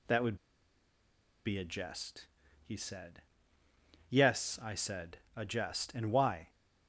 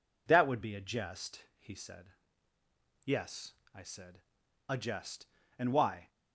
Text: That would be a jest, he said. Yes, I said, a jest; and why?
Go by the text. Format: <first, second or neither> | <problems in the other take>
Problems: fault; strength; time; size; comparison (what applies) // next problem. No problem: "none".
second | pauses between "would" and "be"; at 0.3 s; 1.0 s long